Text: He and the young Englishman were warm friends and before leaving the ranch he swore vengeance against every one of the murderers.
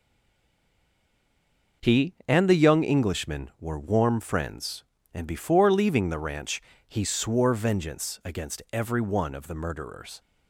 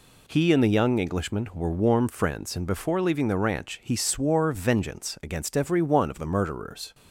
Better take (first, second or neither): second